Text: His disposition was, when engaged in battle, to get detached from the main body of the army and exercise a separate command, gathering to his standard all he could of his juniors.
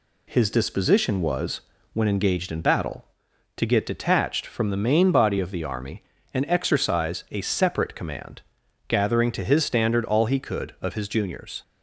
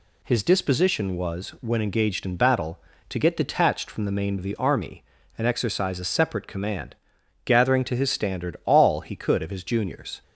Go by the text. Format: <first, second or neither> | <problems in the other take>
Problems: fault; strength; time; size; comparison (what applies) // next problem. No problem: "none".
first | skips "body"; at 4.3 s